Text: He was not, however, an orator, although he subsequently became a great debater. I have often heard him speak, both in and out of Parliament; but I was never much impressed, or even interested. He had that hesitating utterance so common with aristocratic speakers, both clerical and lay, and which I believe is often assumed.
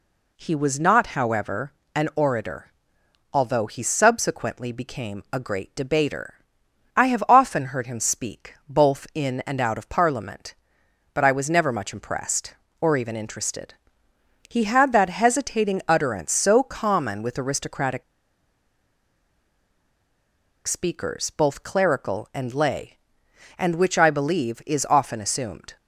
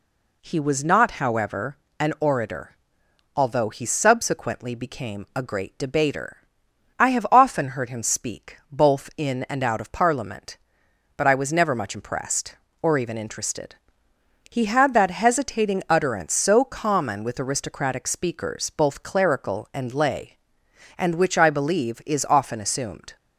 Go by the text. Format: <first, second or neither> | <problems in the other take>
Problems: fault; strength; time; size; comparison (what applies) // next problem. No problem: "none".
second | pauses between "aristocratic" and "speakers"; strong; at 18.0 s; 2.6 s long